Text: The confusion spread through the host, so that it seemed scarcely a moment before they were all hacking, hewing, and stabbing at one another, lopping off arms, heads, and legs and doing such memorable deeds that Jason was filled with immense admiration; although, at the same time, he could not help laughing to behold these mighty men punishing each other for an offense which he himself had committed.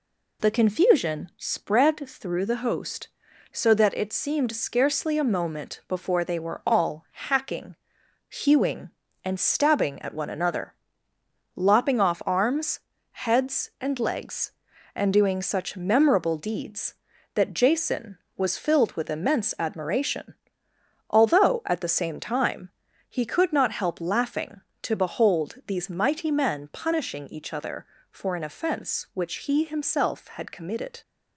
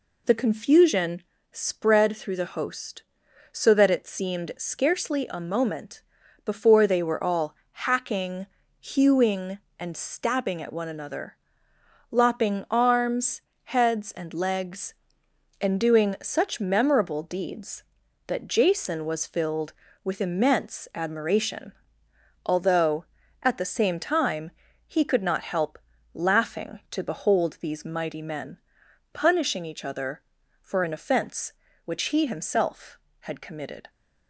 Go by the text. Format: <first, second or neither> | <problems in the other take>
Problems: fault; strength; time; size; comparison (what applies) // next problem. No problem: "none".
first | pauses between "confusion" and "spread"; slight; at 1.2 s; 0.30 s long // pauses between "moment" and "before"; at 6.0 s; 0.44 s long // pauses between "all" and "hacking"; slight; at 7.5 s; 0.18 s long // skips "off"; at 12.6 s // pauses between "help" and "laughing"; slight; at 25.7 s; 0.34 s long // pauses between "men" and "punishing"; noticeable; at 28.5 s; 0.54 s long